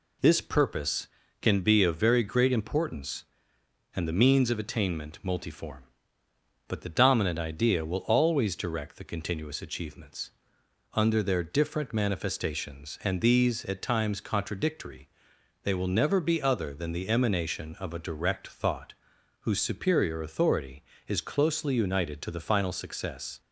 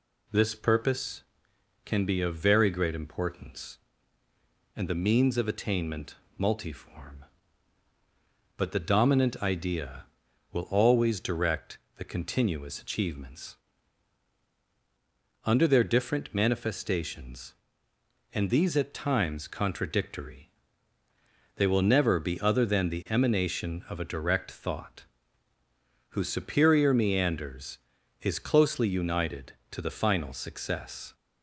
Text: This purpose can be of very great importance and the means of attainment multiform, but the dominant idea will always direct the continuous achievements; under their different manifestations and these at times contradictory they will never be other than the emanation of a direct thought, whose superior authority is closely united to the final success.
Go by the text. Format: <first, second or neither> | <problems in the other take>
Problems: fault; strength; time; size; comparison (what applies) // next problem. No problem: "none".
first | pauses between "attainment" and "multiform"; slight; at 6.1 s; 0.20 s long // pauses between "direct" and "the"; slight; at 11.7 s; 0.18 s long // pauses between "contradictory" and "they"; at 20.4 s; 1.0 s long; noticeable in the first // says "meanders" for "authority"; at 26.9 s